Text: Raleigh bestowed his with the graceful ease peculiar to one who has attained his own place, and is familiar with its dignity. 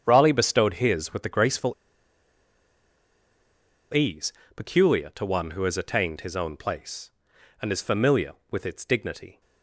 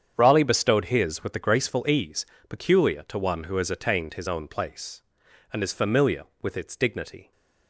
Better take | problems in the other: second | starts louder than the rest; strong; until 1.0 s; 8 dB; strong in the second // pauses between "graceful" and "ease"; strong; at 1.7 s; 2.2 s long // pauses between "ease" and "peculiar"; slight; at 4.3 s; 0.22 s long; slight in the second

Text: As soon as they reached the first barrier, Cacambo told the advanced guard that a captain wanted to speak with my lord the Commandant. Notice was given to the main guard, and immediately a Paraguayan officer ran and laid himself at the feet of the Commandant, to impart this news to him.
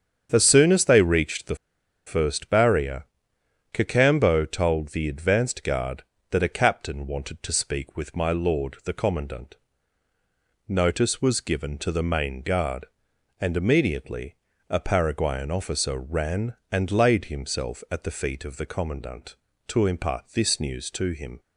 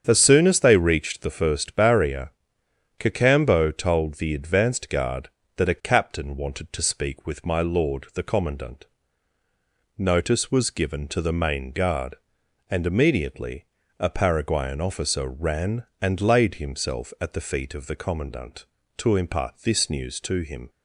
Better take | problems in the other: second | starts louder than the rest; strong; until 1.3 s; 8 dB; strong in the second // pauses between "the" and "first"; noticeable; at 1.5 s; 0.49 s long // pauses between "immediately" and "a"; slight; at 14.3 s; 0.34 s long; slight in the second

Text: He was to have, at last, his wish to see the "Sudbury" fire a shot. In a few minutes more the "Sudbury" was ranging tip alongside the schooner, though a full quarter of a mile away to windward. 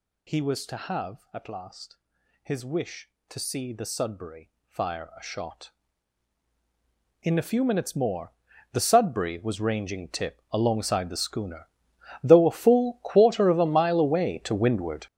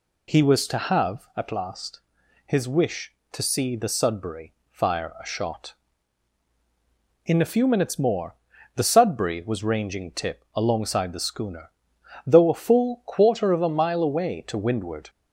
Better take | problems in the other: second | gets louder; strong; throughout; 11.5 dB // pauses between "Sudbury" and "fire"; slight; at 4.5 s; 0.16 s long; slight in the second // pauses between "more" and "the"; at 8.3 s; 0.40 s long; also in the second

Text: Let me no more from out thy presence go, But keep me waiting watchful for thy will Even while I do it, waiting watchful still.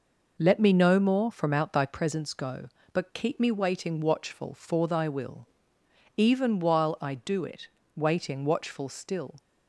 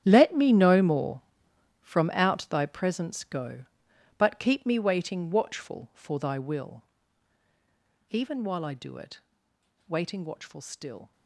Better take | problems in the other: first | gets quieter; strong; throughout; 15 dB // pauses between "will" and "Even"; strong; at 6.8 s; 1.2 s long; noticeable in the first

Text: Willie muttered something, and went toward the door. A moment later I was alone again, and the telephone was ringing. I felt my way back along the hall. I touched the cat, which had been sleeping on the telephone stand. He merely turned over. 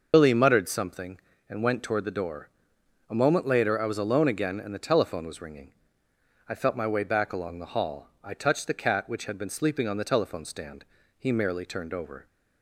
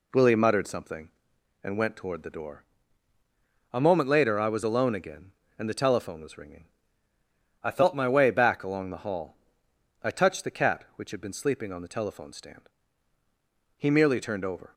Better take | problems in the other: second | loses the start of "Willie"; at 0.1 s; 125 ms

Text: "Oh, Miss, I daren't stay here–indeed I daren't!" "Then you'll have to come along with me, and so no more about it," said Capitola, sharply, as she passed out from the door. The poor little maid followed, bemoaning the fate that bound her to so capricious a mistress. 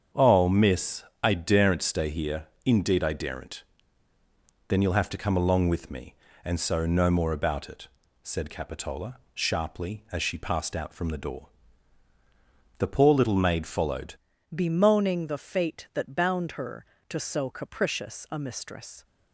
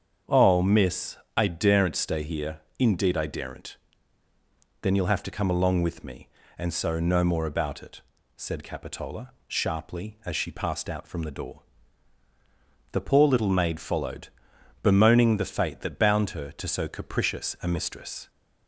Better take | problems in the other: second | starts louder than the rest; strong; until 1.3 s; 7.5 dB; strong in the second // changes voice at "bemoaning"; from 14.5 s on; 4.5 s long

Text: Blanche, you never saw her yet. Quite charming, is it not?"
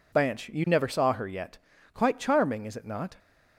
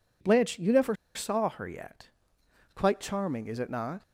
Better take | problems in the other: first | pauses between "never" and "saw"; slight; at 0.9 s; 0.20 s long

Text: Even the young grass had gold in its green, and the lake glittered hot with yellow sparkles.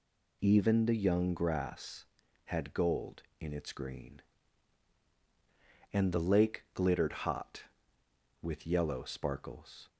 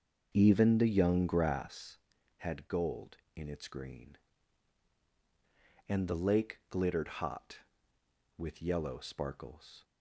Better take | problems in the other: first | starts louder than the rest; until 1.8 s; 6.5 dB

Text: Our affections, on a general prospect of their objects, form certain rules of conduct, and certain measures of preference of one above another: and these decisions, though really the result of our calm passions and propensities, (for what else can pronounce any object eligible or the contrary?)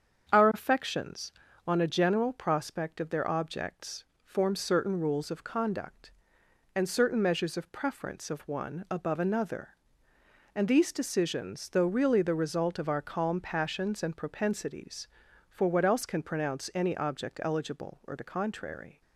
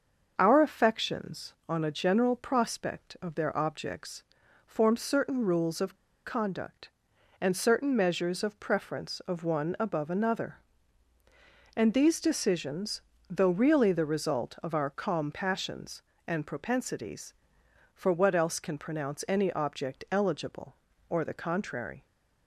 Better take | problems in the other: first | starts louder than the rest; until 1.3 s; 6.5 dB; strong in the first // pauses between "of" and "conduct"; slight; at 5.9 s; 0.33 s long

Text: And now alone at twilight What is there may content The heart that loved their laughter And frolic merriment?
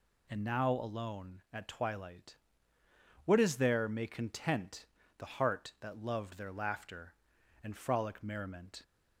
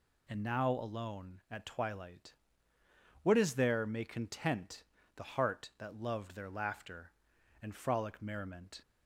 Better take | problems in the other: neither | pauses between "twilight" and "What"; noticeable; the same in both // pauses between "content" and "The"; slight; the same in both

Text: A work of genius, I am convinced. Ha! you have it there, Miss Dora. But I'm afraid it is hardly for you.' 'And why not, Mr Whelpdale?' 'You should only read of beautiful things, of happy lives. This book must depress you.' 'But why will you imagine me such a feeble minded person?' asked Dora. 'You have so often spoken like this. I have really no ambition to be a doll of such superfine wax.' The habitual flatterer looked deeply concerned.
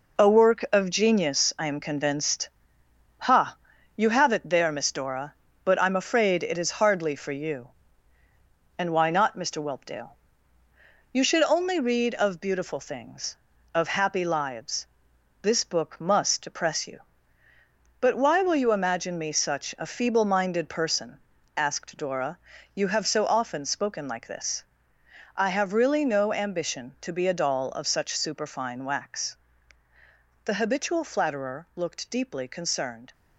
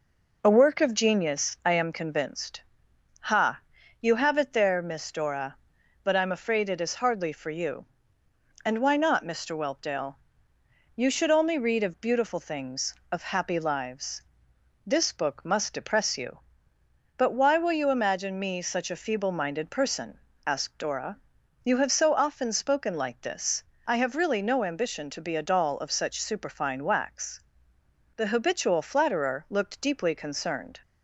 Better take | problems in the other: second | gets quieter; throughout; 6.5 dB

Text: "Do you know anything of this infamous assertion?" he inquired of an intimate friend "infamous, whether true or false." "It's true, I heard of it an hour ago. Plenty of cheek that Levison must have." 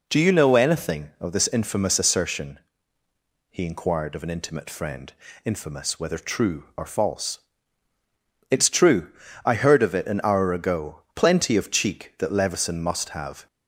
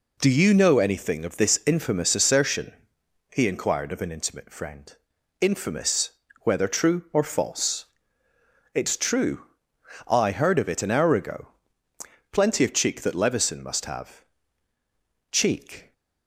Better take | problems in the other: first | pauses between "friend" and "infamous"; noticeable; at 4.9 s; 0.48 s long; slight in the first // goes on to say "Cheek"; noticeable; from 15.3 s on; 0.62 s long

